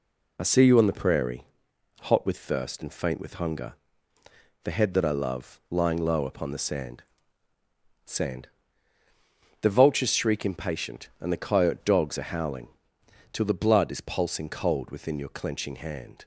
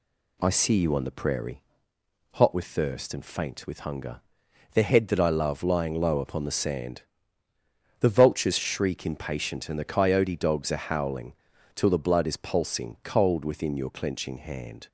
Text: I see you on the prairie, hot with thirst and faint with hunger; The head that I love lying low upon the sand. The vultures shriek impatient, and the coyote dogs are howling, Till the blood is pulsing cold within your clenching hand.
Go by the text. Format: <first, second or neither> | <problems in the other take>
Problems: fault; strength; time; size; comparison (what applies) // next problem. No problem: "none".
second | says "sand" twice; at 8.0 s